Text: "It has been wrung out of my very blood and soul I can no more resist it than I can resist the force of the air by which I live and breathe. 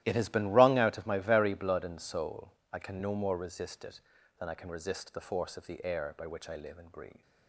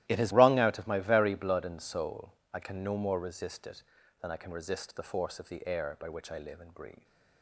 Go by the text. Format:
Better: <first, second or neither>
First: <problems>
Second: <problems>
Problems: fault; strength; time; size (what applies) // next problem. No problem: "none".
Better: first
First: starts louder than the rest; strong; until 1.0 s; 13.5 dB // pauses between "soul" and "I"; slight; at 2.5 s; 0.22 s long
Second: starts louder than the rest; strong; until 1.1 s; 14.5 dB // skips "been"; at 0.3 s // pauses between "soul" and "I"; slight; at 2.3 s; 0.22 s long